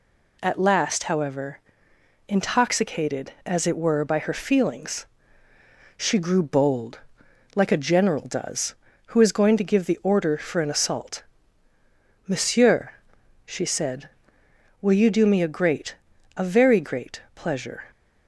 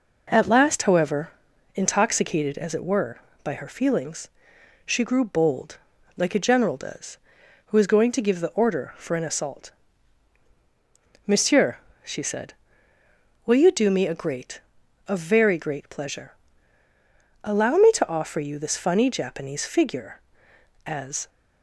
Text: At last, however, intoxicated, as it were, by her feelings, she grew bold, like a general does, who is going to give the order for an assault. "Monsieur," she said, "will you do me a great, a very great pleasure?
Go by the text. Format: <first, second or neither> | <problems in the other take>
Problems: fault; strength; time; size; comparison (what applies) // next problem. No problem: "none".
first | goes on to say "Allow me to offer you this funny Japanese figure as"; strong; from 17.4 s on; 3.8 s long